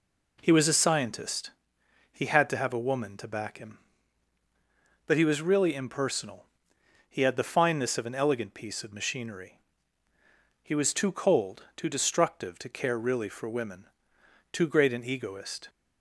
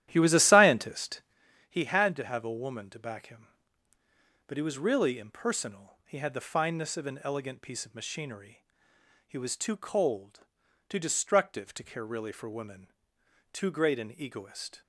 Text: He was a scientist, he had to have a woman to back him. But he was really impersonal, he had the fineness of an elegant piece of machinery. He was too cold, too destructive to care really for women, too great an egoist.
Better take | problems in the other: first | starts louder than the rest; strong; until 1.6 s; 12.5 dB

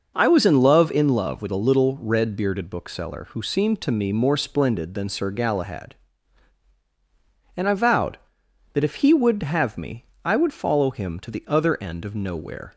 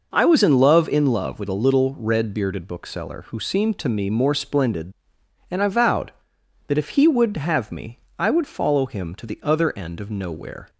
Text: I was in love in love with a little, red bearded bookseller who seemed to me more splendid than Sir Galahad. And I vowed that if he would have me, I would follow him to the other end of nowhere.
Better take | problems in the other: first | skips "than Sir Galahad"; at 5.2 s

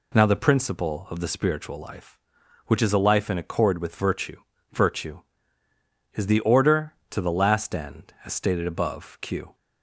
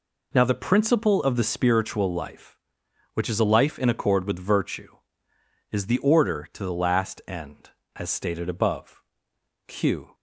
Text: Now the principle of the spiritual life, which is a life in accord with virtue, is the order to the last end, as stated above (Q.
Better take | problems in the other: second | says "virtue" twice; at 4.7 s

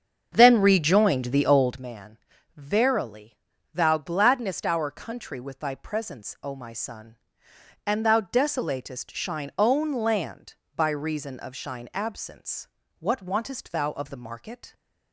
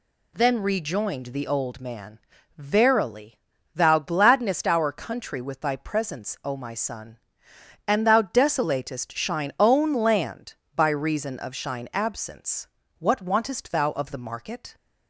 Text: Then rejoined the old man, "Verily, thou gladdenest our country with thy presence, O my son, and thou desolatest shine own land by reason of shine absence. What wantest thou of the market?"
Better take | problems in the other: second | starts louder than the rest; strong; until 1.9 s; 7 dB

